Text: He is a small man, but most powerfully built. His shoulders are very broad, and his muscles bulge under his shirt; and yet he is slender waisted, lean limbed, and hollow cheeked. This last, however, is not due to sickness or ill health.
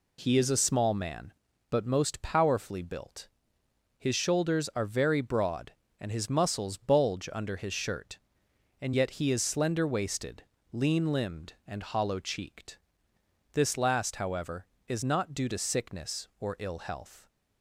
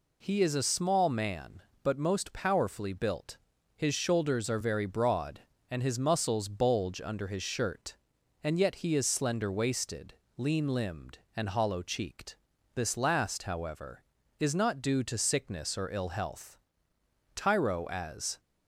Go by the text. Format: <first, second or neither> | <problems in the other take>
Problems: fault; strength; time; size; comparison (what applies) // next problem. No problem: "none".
first | goes on to say "Tyro as"; noticeable; from 17.3 s on; 1.0 s long